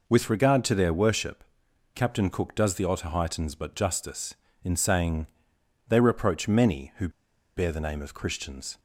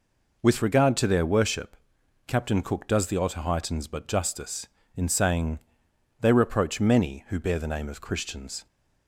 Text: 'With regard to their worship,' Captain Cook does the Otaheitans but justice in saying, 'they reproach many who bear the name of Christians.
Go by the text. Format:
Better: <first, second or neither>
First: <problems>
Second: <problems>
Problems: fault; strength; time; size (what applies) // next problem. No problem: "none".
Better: second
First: pauses between "who" and "bear"; noticeable; at 7.0 s; 0.47 s long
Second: none